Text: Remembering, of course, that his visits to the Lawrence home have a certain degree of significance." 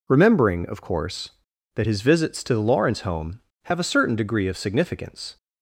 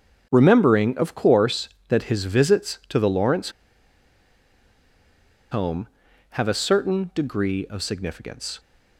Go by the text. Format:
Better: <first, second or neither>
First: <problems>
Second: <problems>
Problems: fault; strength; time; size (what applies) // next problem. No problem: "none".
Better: first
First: none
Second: starts louder than the rest; strong; until 1.3 s; 7.5 dB // pauses between "Lawrence" and "home"; strong; at 3.5 s; 2.0 s long